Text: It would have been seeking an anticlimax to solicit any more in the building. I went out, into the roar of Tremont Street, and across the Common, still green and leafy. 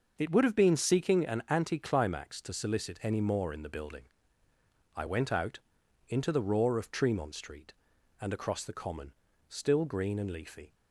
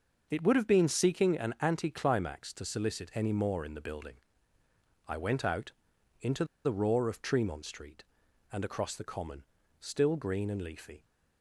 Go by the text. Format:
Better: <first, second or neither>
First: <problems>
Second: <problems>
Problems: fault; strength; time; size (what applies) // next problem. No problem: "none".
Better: first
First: starts louder than the rest; until 1.1 s; 6.5 dB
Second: starts louder than the rest; until 1.3 s; 6.5 dB // pauses between "into" and "the"; slight; at 6.4 s; 0.20 s long